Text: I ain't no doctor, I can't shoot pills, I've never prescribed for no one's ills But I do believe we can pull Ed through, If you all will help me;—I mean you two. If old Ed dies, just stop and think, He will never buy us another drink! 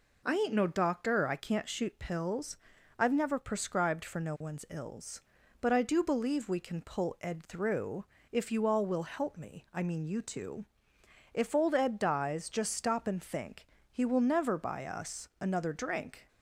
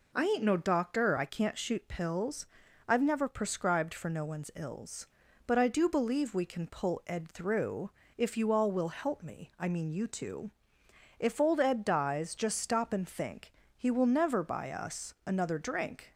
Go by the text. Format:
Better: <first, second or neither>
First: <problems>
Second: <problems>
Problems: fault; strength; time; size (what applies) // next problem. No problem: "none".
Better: neither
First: none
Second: none